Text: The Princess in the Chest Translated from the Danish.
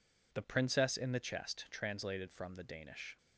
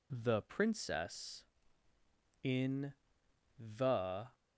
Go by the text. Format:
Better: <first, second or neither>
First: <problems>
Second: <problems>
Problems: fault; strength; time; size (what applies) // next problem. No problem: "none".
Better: first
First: none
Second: pauses between "in" and "the"; noticeable; at 2.9 s; 0.64 s long // stops before "Chest Translated from the Danish"; at 4.3 s